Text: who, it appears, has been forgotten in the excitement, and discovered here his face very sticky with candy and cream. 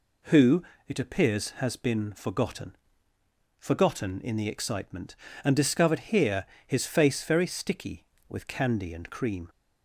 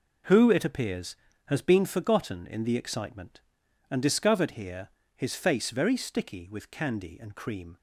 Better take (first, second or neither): second